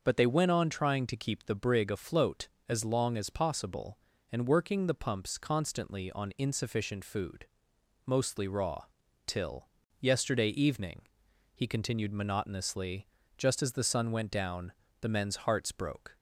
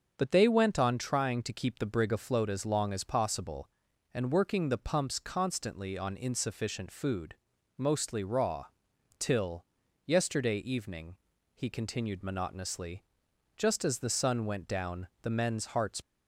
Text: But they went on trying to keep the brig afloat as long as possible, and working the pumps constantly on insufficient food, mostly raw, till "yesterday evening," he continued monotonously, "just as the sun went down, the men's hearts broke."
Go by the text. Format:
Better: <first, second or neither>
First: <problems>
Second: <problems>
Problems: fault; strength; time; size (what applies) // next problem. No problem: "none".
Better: first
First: starts louder than the rest; until 1.0 s; 6 dB // pauses between "till" and "yesterday"; slight; at 9.6 s; 0.32 s long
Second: starts louder than the rest; until 1.1 s; 6.5 dB // pauses between "till" and "yesterday"; at 9.6 s; 0.40 s long // stops before "broke"; at 16.0 s